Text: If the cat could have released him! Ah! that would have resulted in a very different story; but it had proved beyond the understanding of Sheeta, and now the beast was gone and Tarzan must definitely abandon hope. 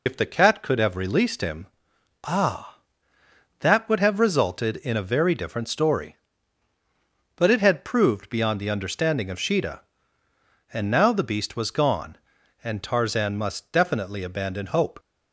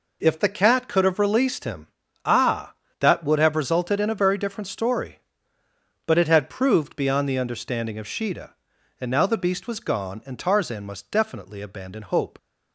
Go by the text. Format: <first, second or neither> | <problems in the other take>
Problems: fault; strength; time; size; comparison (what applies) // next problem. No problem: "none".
second | loses the start of "If"; at 0.0 s; 80 ms